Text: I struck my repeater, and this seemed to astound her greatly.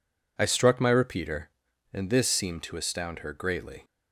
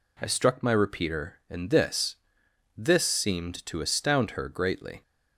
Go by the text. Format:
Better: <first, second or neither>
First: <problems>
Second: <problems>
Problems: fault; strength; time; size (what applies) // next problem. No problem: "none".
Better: first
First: none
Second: says "this" twice; at 2.7 s